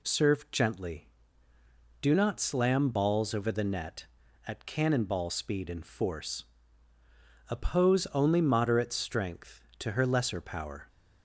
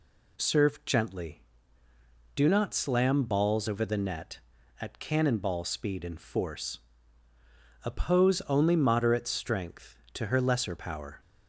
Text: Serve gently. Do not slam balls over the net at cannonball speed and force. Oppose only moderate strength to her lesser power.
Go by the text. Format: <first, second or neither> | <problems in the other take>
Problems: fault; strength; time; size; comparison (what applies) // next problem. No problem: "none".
neither | none